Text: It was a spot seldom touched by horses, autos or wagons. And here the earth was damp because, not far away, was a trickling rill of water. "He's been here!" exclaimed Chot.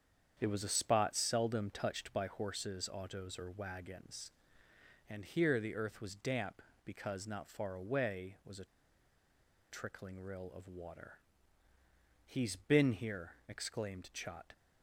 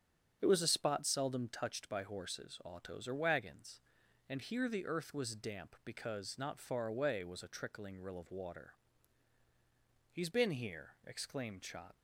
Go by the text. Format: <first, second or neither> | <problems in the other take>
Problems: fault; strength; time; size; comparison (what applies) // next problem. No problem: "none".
second | starts louder than the rest; strong; until 1.3 s; 8 dB; strong in the second // pauses between "a" and "trickling"; at 8.6 s; 1.0 s long